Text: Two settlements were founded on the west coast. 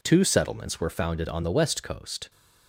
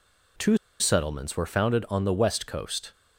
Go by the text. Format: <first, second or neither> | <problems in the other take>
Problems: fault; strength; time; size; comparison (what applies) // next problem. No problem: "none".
first | pauses between "Two" and "settlements"; slight; at 0.5 s; 0.22 s long